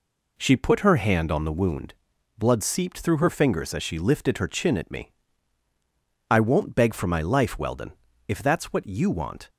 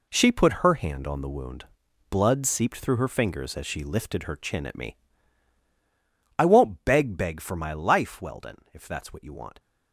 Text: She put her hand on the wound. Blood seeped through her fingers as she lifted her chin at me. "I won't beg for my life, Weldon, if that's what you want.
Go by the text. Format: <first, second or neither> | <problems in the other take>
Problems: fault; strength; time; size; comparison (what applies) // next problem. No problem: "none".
first | says "beg" twice; at 7.1 s